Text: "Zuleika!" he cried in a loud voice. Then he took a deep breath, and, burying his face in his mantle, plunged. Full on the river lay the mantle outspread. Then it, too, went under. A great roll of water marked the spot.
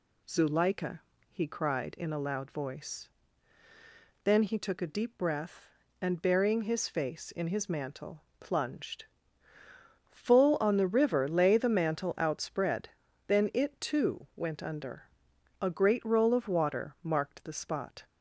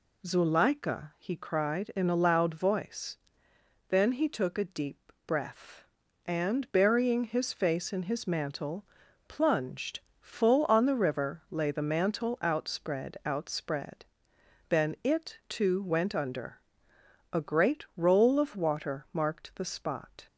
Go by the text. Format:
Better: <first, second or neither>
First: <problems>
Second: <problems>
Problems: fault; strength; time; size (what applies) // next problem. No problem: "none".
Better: first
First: none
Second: says "outspread" twice; at 13.2 s